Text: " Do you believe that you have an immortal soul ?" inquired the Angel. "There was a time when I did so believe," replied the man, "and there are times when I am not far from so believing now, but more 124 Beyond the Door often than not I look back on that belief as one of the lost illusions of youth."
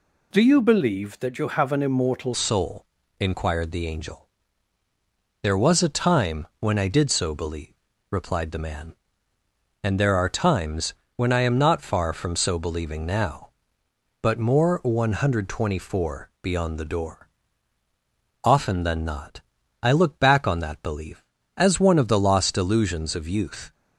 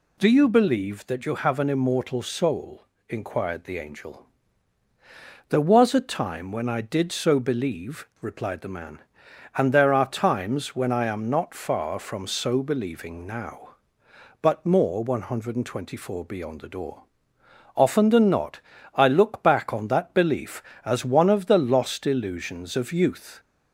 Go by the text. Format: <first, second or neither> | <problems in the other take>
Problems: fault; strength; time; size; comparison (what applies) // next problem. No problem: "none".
second | changes voice at "soul"; from 2.3 s on; 21.4 s long // pauses between "times" and "when"; slight; at 10.9 s; 0.24 s long // pauses between "Door" and "often"; at 17.2 s; 1.1 s long; noticeable in the second // pauses between "not" and "I"; at 19.4 s; 0.42 s long; slight in the second